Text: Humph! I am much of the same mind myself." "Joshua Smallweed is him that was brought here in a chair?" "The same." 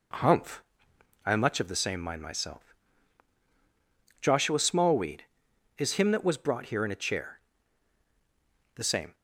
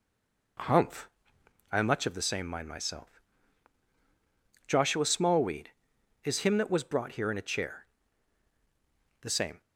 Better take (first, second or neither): first